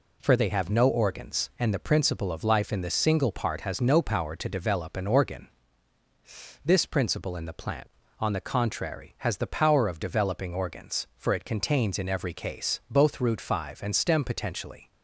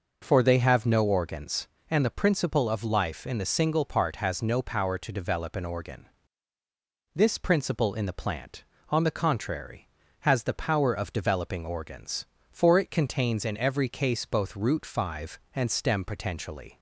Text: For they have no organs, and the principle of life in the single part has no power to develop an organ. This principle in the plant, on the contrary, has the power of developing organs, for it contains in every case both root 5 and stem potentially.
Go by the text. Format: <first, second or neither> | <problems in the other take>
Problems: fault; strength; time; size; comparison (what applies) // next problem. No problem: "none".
neither | none